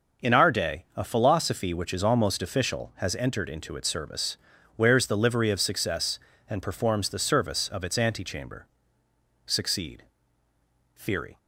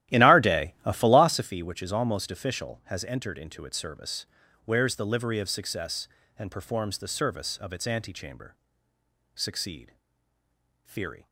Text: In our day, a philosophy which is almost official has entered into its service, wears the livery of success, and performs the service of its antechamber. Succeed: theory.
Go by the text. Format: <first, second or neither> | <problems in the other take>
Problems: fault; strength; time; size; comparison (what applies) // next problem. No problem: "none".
first | starts louder than the rest; strong; until 1.5 s; 13.5 dB